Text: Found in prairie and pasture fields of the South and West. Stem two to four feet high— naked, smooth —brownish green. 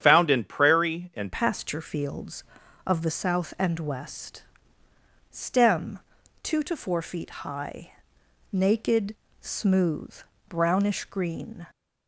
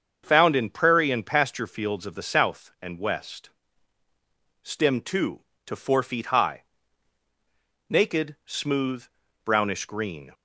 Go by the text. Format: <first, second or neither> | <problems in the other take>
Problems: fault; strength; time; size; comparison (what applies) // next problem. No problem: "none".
second | starts louder than the rest; strong; until 1.0 s; 9 dB; also in the second // changes voice at "pasture"; from 1.3 s on; 10.3 s long // pauses between "Stem" and "two"; at 5.9 s; 0.42 s long